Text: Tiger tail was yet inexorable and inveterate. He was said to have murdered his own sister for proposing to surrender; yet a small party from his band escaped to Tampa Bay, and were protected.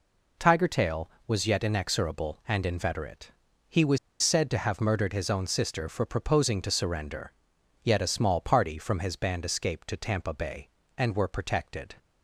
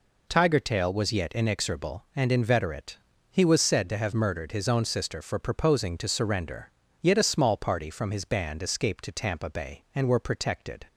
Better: second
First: pauses between "was" and "said"; slight; at 3.9 s; 0.24 s long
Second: none

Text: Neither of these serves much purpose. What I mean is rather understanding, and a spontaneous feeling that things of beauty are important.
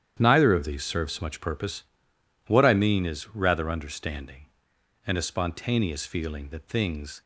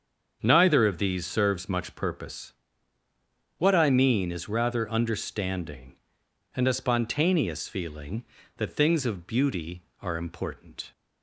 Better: second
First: starts louder than the rest; strong; until 1.2 s; 9.5 dB // stops before "of beauty are important"; at 7.2 s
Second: starts louder than the rest; until 1.4 s; 7 dB

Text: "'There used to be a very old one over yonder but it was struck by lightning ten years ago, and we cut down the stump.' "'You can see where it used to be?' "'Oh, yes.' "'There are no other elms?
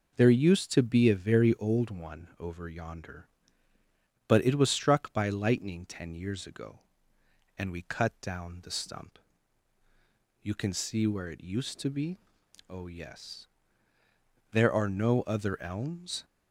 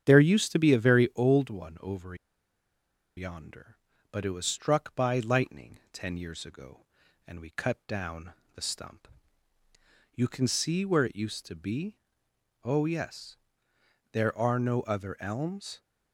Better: first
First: none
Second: starts louder than the rest; strong; until 1.0 s; 8.5 dB // pauses between "over" and "yonder"; at 2.1 s; 1.0 s long // pauses between "down" and "the"; slight; at 8.3 s; 0.22 s long

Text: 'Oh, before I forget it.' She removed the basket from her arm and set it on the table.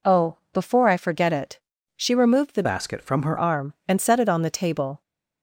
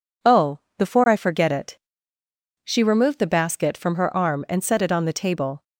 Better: second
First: changes voice from "basket" to "her"; from 2.6 to 3.3 s; 0.7 s long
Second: none

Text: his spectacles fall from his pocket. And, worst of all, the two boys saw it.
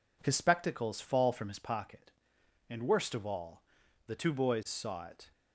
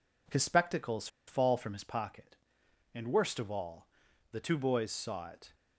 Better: first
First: none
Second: pauses between "spectacles" and "fall"; slight; at 1.0 s; 0.20 s long

